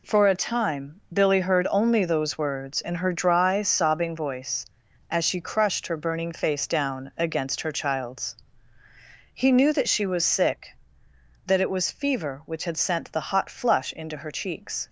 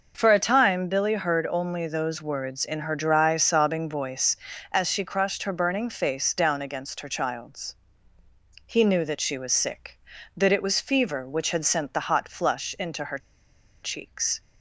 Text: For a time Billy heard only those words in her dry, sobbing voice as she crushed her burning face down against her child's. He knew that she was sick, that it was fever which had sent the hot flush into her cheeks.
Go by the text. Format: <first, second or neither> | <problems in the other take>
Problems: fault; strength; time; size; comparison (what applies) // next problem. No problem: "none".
first | pauses between "her" and "cheeks"; noticeable; at 13.1 s; 0.65 s long